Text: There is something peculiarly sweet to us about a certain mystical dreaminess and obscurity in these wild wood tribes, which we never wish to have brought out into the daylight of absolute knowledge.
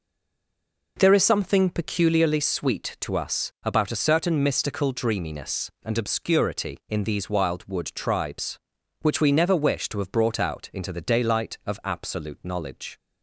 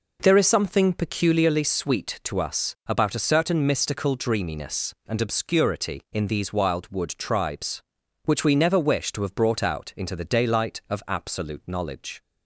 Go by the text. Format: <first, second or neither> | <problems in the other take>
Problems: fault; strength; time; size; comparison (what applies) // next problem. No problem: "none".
second | stays silent before the first word; slight; until 0.9 s; 0.9 s long